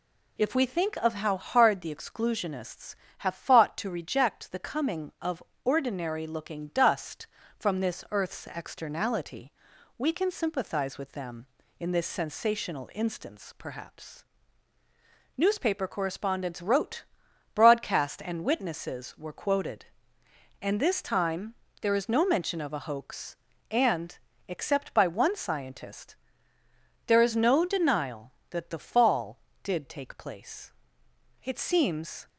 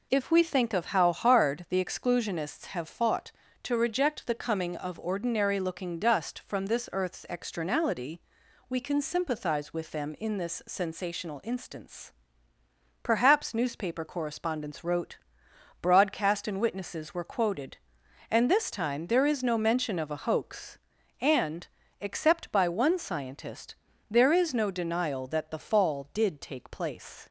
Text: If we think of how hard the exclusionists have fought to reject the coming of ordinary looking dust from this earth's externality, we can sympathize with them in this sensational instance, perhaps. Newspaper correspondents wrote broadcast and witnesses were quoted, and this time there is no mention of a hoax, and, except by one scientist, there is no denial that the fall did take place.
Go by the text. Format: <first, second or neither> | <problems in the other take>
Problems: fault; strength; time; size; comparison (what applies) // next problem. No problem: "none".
second | pauses between "of" and "ordinary"; slight; at 5.4 s; 0.22 s long // pauses between "wrote" and "broadcast"; noticeable; at 17.0 s; 0.50 s long; noticeable in the second // pauses between "time" and "there"; slight; at 21.5 s; 0.26 s long // goes on to say "It seems"; noticeable; from 31.4 s on; 0.86 s long